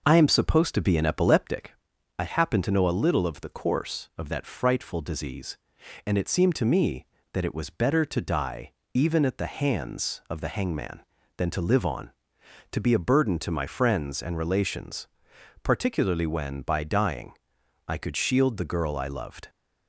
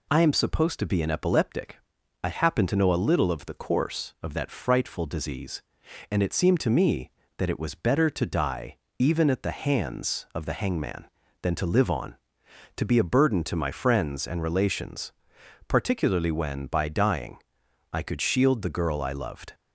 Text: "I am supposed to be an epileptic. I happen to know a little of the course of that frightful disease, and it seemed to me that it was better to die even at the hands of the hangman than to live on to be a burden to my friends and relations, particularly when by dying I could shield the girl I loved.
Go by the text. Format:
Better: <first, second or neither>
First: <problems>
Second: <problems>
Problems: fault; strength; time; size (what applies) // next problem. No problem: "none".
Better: second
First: starts louder than the rest; noticeable; until 1.7 s; 5.5 dB // pauses between "die" and "even"; slight; at 8.7 s; 0.20 s long // pauses between "dying" and "I"; noticeable; at 17.3 s; 0.56 s long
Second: pauses between "die" and "even"; slight; at 8.7 s; 0.20 s long // pauses between "dying" and "I"; noticeable; at 17.3 s; 0.56 s long